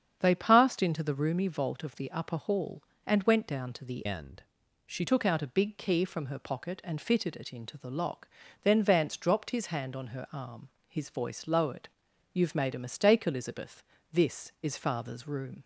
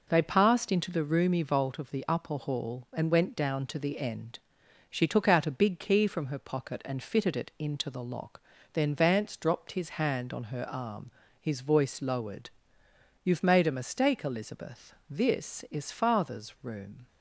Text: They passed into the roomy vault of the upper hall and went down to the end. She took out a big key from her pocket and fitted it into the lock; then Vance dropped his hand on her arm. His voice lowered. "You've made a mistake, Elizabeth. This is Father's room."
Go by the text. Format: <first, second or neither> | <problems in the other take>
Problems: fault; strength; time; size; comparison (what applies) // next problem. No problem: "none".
second | starts louder than the rest; strong; until 1.2 s; 8 dB // changes voice from "end" to "She"; from 4.0 to 5.0 s; 1.0 s long